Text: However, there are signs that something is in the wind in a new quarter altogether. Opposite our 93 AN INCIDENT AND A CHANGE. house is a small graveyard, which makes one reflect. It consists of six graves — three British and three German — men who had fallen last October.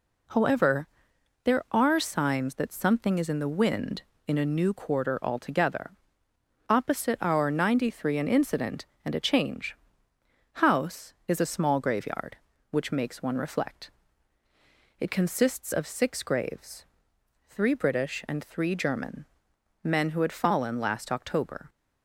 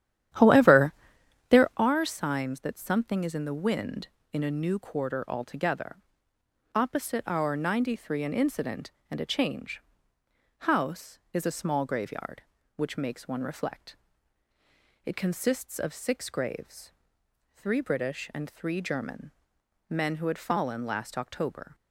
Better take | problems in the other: first | starts louder than the rest; strong; until 1.9 s; 11 dB

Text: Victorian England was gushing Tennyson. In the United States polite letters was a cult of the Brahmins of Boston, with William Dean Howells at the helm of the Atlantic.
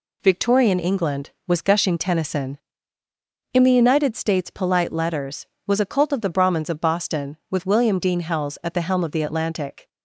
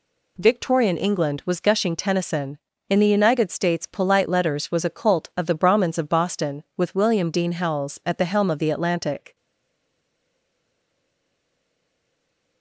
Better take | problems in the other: first | stays silent after the last word; strong; from 9.3 s on; 3.3 s long

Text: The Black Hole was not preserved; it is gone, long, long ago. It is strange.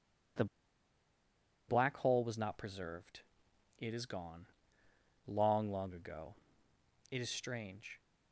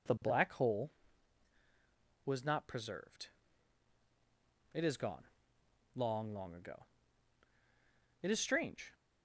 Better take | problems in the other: second | pauses between "The" and "Black"; at 0.4 s; 1.2 s long

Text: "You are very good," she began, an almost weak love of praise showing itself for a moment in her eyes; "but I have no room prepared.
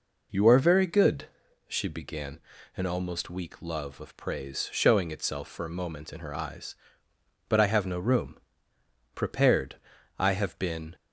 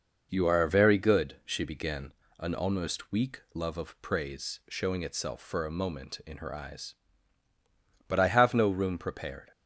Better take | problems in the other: second | pauses between "room" and "prepared"; noticeable; at 8.3 s; 0.86 s long // goes on to say "I have been"; noticeable; from 10.1 s on; 0.78 s long

